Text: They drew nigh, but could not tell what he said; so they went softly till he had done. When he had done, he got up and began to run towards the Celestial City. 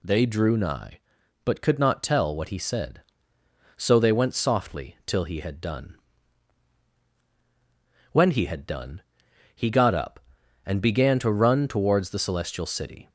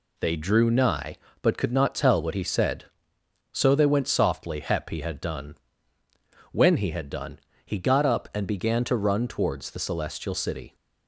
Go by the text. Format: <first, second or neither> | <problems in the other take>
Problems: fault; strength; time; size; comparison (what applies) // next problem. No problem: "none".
first | says "hep" for "till"; at 4.6 s